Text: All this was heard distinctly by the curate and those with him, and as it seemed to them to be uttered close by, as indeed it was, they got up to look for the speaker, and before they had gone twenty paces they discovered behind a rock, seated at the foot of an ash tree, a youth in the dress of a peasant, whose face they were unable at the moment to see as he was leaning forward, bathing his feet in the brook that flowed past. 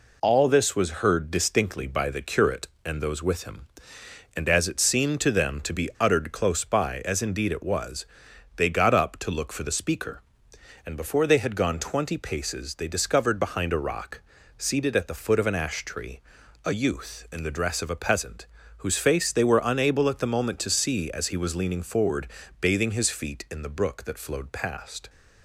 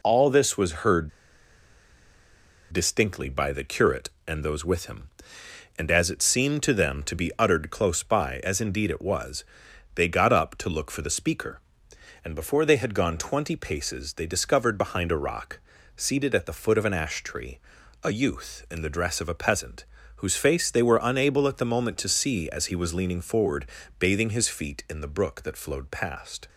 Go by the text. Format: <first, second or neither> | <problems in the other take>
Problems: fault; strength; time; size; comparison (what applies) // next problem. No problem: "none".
first | pauses between "heard" and "distinctly"; strong; at 1.1 s; 1.6 s long